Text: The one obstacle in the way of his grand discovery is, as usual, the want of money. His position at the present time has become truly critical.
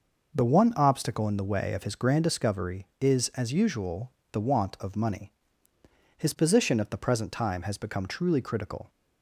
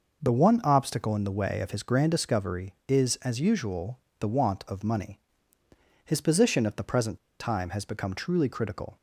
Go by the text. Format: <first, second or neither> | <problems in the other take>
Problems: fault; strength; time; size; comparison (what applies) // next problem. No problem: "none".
first | pauses between "present" and "time"; slight; at 7.1 s; 0.22 s long